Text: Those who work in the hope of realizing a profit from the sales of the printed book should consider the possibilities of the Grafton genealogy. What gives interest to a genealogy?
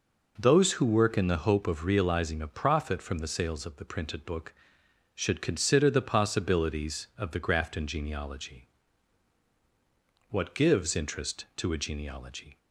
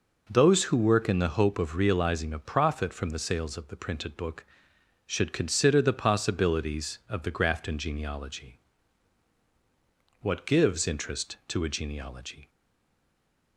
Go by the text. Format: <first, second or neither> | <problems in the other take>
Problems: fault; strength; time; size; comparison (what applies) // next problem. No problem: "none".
first | stays silent after the last word; from 12.4 s on; 1.1 s long